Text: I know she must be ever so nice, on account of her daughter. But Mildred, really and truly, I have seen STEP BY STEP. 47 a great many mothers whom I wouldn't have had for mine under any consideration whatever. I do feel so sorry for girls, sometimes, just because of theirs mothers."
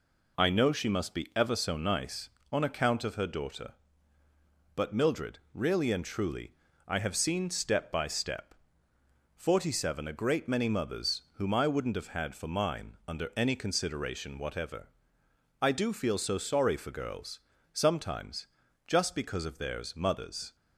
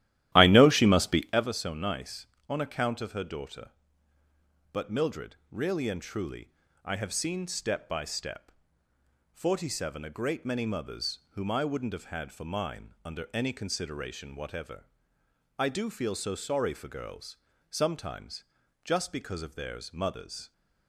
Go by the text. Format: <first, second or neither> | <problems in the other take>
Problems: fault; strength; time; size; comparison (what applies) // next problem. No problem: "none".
first | starts louder than the rest; strong; until 1.5 s; 14 dB